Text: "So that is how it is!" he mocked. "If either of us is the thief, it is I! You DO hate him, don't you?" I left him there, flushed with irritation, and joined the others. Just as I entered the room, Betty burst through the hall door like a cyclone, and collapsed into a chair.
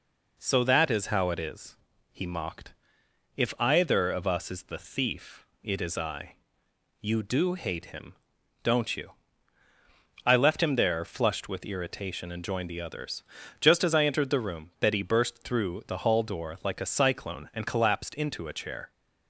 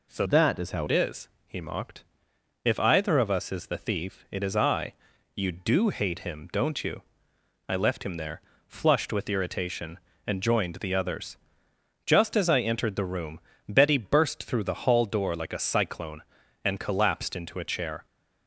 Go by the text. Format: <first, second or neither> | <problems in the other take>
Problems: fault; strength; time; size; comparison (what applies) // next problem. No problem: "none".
first | changes voice from "that" to "how"; from 0.2 to 0.8 s; 0.6 s long